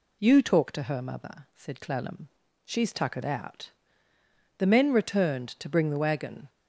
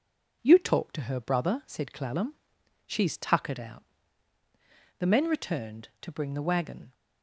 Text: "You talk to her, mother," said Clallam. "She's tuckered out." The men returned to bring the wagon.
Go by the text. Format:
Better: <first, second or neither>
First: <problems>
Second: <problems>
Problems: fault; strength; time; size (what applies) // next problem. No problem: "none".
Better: first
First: none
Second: says "brother" for "mother"; at 1.1 s